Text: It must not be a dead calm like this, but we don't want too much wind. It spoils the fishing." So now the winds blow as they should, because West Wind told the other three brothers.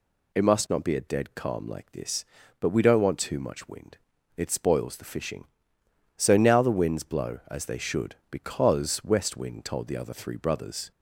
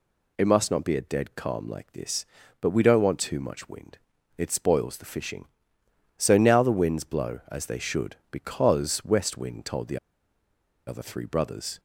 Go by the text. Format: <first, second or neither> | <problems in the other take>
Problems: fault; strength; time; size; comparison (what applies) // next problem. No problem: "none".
first | pauses between "the" and "other"; noticeable; at 9.9 s; 0.90 s long